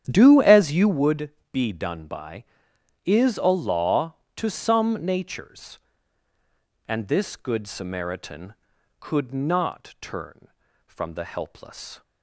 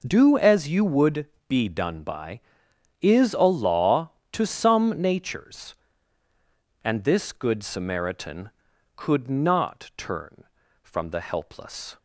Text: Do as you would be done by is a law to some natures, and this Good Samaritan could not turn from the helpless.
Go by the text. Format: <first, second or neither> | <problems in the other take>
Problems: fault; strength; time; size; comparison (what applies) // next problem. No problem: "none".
second | starts louder than the rest; strong; until 1.0 s; 9.5 dB // pauses between "would" and "be"; slight; at 1.3 s; 0.20 s long; slight in the second